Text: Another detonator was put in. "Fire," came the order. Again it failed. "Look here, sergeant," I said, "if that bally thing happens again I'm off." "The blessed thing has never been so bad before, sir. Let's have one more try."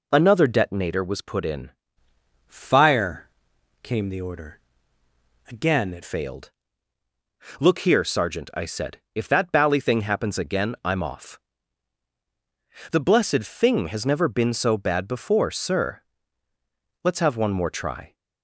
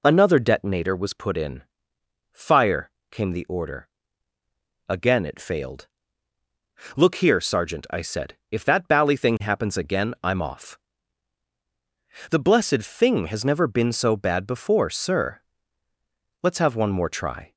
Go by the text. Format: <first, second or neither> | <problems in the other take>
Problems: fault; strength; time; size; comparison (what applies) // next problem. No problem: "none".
second | changes voice from "Fire" to "it"; from 2.4 to 6.0 s; 3.6 s long